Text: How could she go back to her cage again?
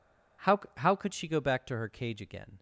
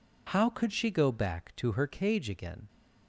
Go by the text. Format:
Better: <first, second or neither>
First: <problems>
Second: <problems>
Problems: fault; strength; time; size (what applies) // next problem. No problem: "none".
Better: second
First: says "How" twice; at 0.7 s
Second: none